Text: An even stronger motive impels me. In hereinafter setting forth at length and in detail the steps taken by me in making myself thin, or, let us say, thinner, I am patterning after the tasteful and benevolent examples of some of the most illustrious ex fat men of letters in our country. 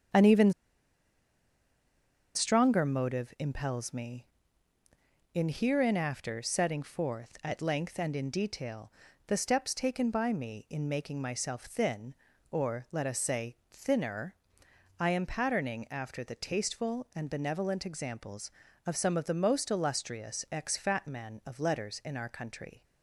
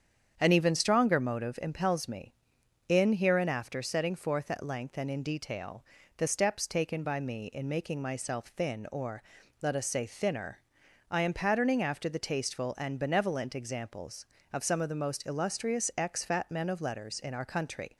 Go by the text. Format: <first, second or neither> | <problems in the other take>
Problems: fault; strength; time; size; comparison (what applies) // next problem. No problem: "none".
second | starts louder than the rest; strong; until 2.9 s; 8 dB; strong in the second // pauses between "even" and "stronger"; strong; at 0.5 s; 1.8 s long // pauses between "detail" and "the"; slight; at 8.9 s; 0.36 s long; slight in the second